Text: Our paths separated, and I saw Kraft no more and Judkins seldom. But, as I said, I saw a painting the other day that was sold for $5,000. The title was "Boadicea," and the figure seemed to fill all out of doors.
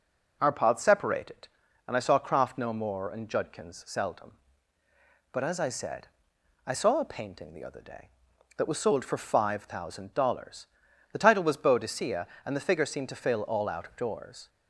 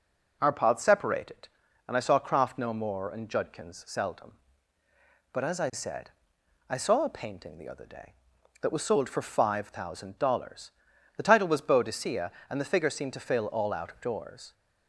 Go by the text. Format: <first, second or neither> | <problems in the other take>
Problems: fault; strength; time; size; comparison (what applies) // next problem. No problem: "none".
neither | none